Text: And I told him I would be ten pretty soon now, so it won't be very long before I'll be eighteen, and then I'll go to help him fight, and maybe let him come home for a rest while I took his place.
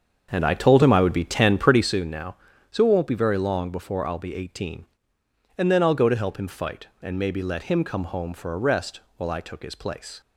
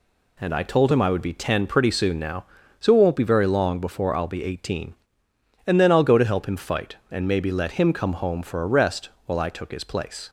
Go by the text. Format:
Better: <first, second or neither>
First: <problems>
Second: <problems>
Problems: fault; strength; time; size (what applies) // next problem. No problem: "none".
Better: second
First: starts louder than the rest; strong; until 2.0 s; 7 dB // pauses between "rest" and "while"; slight; at 9.0 s; 0.16 s long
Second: pauses between "rest" and "while"; slight; at 9.0 s; 0.16 s long